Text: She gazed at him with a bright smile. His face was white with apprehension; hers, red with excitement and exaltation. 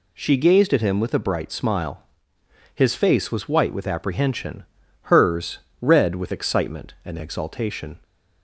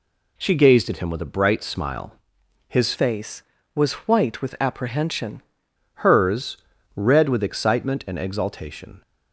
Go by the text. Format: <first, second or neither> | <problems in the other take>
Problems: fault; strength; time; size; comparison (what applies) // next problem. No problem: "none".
first | changes voice from "face" to "apprehension"; from 2.9 to 5.4 s; 2.5 s long